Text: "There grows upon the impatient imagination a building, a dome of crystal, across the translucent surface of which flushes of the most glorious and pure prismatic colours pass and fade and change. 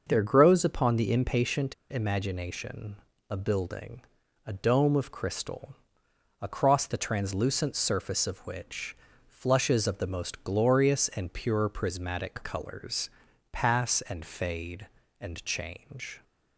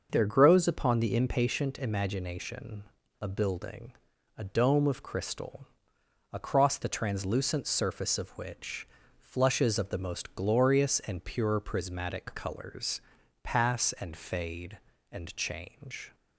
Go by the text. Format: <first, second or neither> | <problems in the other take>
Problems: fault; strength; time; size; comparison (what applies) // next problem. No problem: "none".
second | starts louder than the rest; until 1.0 s; 6 dB; also in the second // pauses between "impatient" and "imagination"; slight; at 1.7 s; 0.16 s long // pauses between "imagination" and "a"; slight; at 2.9 s; 0.34 s long; also in the second // pauses between "which" and "flushes"; slight; at 8.9 s; 0.32 s long; slight in the second // pauses between "colours" and "pass"; at 13.0 s; 0.42 s long; also in the second